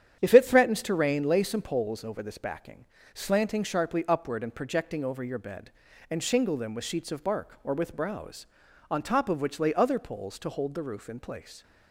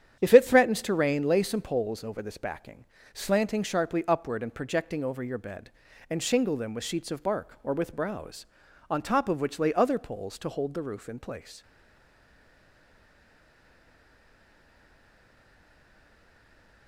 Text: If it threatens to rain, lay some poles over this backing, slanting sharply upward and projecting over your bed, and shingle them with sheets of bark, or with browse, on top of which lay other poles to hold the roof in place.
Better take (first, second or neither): first